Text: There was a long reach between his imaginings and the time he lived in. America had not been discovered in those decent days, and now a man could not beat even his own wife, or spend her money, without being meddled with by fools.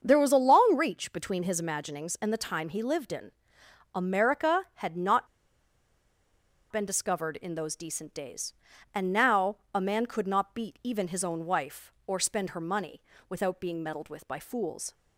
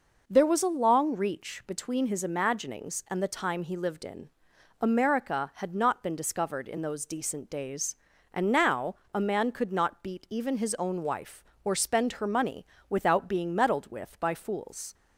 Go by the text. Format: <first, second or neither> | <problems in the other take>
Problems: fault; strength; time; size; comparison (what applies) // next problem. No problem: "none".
second | starts louder than the rest; until 1.0 s; 7 dB // pauses between "not" and "been"; strong; at 5.2 s; 1.4 s long // pauses between "now" and "a"; slight; at 9.5 s; 0.18 s long; slight in the second